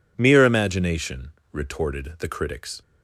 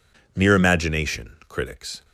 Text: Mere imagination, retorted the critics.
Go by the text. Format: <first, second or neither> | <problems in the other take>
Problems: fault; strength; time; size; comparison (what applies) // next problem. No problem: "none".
first | skips "retorted the"; at 1.3 s